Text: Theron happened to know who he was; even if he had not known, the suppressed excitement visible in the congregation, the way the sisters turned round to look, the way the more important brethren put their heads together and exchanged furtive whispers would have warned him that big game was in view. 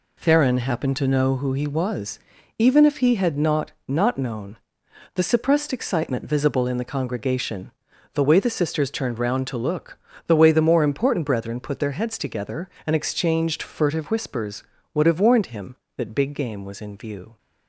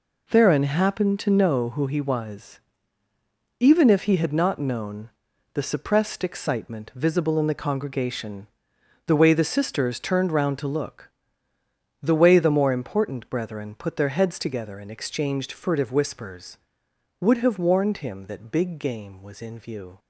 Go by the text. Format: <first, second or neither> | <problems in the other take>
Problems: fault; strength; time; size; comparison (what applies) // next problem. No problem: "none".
second | says "not" twice; at 3.8 s